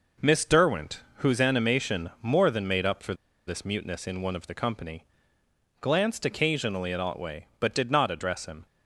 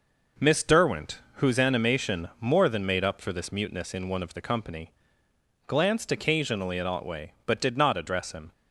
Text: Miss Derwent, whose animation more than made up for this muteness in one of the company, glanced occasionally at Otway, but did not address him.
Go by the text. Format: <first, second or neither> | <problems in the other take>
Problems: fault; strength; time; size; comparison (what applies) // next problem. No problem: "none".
second | pauses between "for" and "this"; slight; at 3.1 s; 0.32 s long